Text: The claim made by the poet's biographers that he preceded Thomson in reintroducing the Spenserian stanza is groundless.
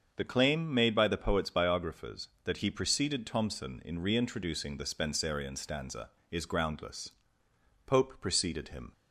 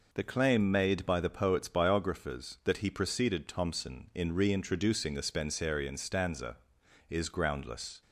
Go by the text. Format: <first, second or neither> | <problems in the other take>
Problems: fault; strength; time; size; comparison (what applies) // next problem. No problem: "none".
second | starts louder than the rest; until 1.1 s; 6.5 dB // goes on to say "Pope preceded him"; noticeable; from 7.8 s on; 1.0 s long